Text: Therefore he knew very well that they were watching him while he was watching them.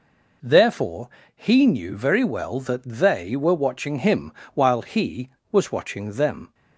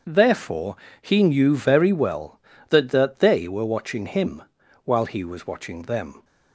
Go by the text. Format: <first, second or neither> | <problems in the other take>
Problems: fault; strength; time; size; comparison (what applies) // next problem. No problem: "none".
first | starts louder than the rest; until 1.3 s; 7 dB // pauses between "Therefore" and "he"; slight; at 0.7 s; 0.26 s long; slight in the first // says "that" twice; at 2.8 s // pauses between "him" and "while"; at 4.4 s; 0.40 s long; slight in the first